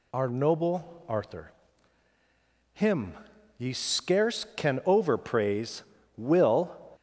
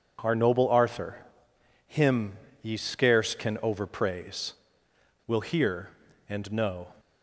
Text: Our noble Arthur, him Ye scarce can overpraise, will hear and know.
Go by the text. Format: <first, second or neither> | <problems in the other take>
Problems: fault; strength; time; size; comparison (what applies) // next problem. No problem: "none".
second | pauses between "him" and "Ye"; noticeable; at 3.1 s; 0.46 s long; slight in the second // stops before "hear and know"; at 6.9 s